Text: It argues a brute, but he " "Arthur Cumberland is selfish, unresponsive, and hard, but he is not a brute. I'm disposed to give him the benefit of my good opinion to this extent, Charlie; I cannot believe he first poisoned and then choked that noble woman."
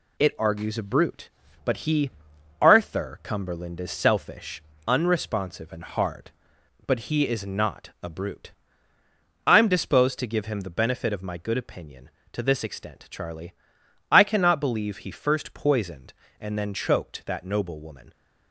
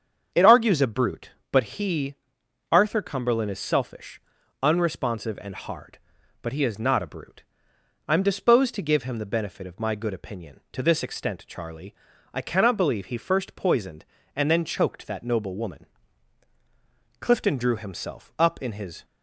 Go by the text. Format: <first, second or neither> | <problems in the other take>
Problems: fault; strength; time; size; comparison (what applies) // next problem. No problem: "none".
first | starts louder than the rest; strong; until 1.5 s; 7 dB // goes on to say "Clifton drew himself up in his"; strong; from 17.2 s on; 1.8 s long